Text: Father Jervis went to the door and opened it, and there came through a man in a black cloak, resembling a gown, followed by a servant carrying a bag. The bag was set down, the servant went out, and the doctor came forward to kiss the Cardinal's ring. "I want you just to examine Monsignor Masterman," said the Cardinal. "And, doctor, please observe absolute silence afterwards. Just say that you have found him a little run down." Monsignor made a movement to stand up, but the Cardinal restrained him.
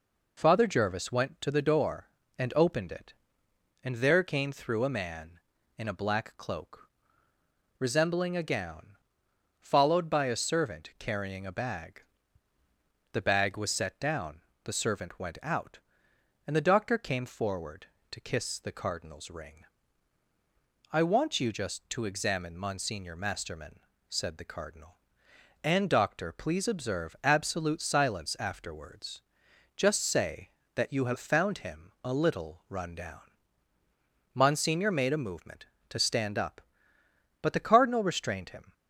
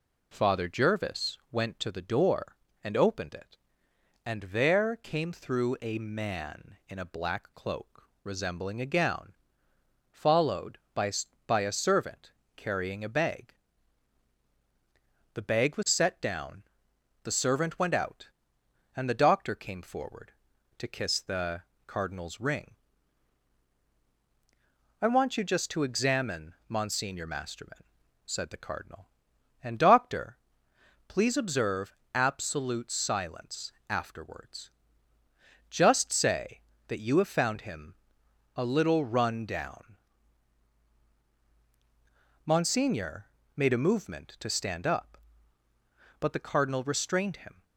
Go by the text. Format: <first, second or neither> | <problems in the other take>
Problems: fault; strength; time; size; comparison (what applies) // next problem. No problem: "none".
first | says "by" twice; at 11.4 s // pauses between "servant" and "carrying"; slight; at 12.3 s; 0.26 s long // pauses between "the" and "Cardinal's"; slight; at 21.6 s; 0.26 s long // pauses between "observe" and "absolute"; slight; at 31.9 s; 0.18 s long // pauses between "silence" and "afterwards"; slight; at 33.7 s; 0.16 s long // pauses between "him" and "a"; noticeable; at 37.9 s; 0.60 s long // pauses between "Monsignor" and "made"; slight; at 43.3 s; 0.26 s long